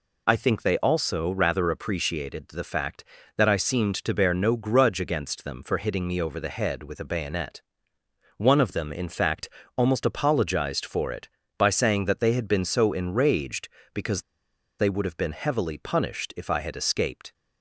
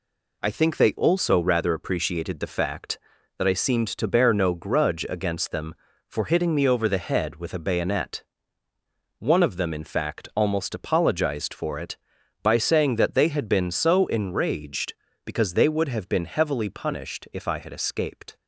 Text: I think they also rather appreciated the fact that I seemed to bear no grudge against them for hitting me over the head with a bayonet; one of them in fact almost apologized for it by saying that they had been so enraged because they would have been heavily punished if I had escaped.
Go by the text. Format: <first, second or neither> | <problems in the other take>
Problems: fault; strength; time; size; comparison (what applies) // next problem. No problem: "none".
second | pauses between "fact" and "almost"; slight; at 9.4 s; 0.26 s long // pauses between "because" and "they"; noticeable; at 14.2 s; 0.57 s long